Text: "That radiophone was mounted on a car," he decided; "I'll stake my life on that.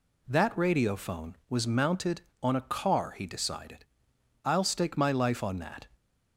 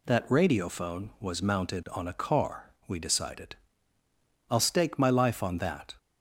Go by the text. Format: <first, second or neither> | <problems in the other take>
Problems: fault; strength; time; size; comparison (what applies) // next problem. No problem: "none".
first | says "we" for "he"; at 2.8 s